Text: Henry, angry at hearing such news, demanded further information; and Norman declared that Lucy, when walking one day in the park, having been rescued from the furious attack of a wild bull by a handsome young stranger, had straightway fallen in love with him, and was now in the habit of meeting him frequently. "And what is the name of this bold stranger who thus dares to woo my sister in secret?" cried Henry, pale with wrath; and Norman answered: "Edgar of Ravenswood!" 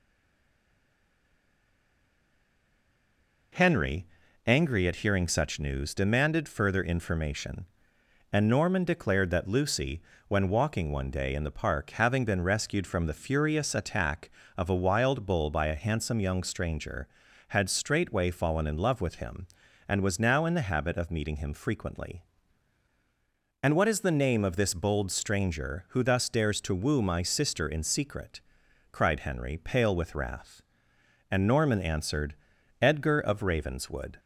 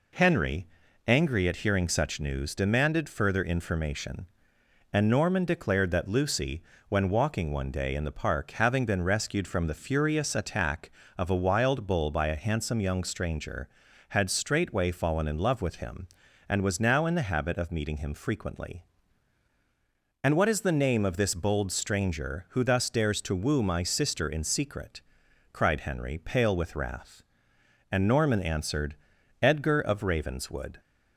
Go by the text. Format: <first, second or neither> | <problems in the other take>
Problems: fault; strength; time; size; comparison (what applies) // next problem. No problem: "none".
second | stays silent before the first word; strong; until 3.5 s; 3.5 s long